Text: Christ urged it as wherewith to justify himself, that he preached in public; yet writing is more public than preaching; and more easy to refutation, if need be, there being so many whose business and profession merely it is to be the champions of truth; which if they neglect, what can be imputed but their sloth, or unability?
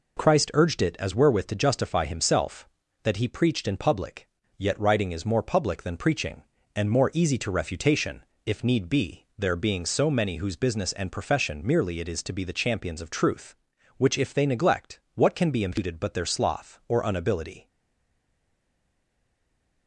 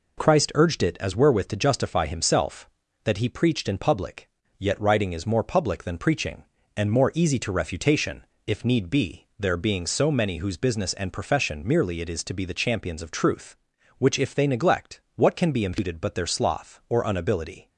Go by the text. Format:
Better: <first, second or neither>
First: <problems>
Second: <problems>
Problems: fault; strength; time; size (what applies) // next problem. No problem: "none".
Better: second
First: stays silent after the last word; from 17.6 s on; 2.2 s long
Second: none